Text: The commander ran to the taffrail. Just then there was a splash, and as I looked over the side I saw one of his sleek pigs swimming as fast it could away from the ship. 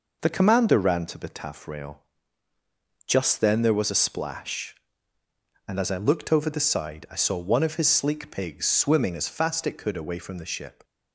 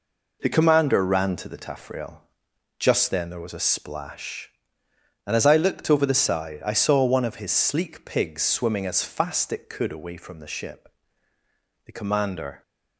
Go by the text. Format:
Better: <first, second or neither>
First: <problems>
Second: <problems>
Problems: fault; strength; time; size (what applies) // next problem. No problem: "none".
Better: first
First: none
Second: goes on to say "The commander"; noticeable; from 11.8 s on; 0.78 s long